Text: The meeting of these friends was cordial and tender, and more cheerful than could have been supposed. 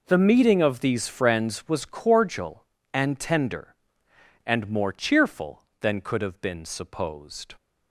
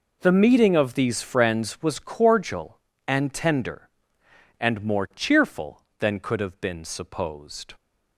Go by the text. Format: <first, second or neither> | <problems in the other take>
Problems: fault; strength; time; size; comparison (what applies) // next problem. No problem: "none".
neither | none